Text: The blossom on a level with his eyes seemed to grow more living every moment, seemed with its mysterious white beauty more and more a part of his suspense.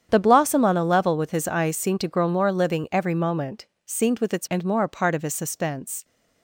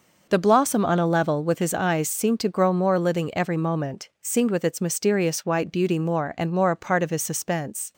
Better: second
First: starts louder than the rest; strong; until 1.1 s; 8.5 dB // skips "mysterious white beauty more"; at 4.4 s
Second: none

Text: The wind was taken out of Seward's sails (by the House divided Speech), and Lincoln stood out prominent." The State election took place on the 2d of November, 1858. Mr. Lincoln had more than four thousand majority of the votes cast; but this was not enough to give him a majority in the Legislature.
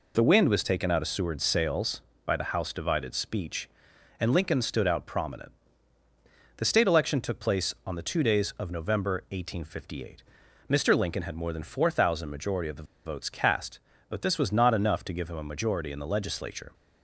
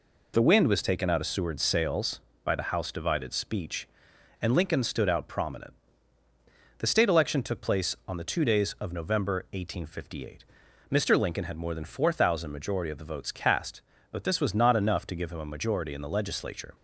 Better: second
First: pauses between "the" and "votes"; slight; at 12.8 s; 0.21 s long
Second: none

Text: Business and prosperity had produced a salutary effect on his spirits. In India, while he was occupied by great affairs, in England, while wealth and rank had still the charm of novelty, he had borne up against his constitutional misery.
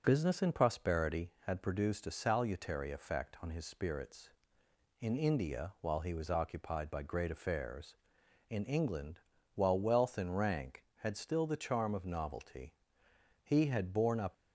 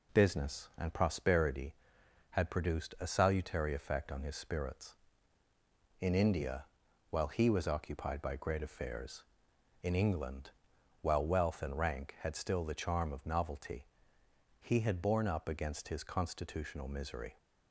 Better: second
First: stops before "against his constitutional misery"; at 14.3 s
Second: none

